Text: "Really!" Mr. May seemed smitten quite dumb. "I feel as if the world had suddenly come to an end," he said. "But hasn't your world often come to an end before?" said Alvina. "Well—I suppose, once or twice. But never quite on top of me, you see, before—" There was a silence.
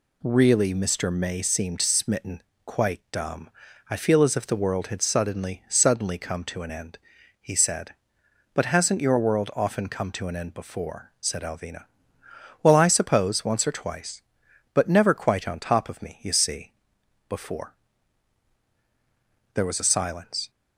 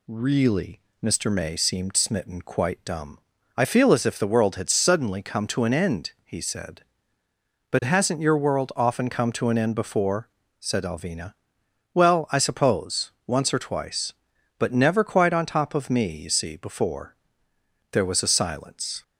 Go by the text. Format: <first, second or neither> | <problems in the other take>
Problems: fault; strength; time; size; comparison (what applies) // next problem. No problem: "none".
second | pauses between "smitten" and "quite"; slight; at 2.4 s; 0.24 s long // says "suddenly" twice; at 5.6 s